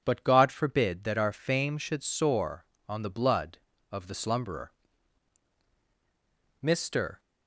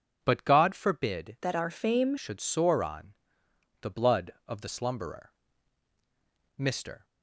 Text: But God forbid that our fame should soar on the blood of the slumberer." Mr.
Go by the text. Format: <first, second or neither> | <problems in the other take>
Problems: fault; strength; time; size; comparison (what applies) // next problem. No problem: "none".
first | changes voice from "that" to "fame"; from 1.4 to 2.1 s; 0.7 s long // pauses between "on" and "the"; noticeable; at 3.1 s; 0.68 s long